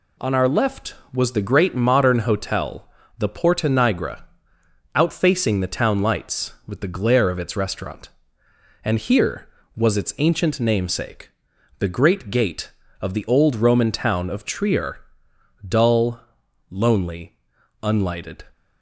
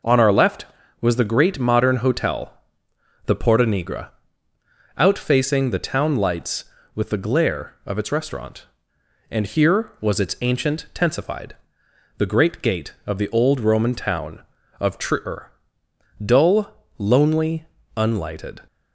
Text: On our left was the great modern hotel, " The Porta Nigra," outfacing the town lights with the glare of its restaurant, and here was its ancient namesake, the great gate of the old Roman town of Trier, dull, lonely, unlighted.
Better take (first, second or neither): first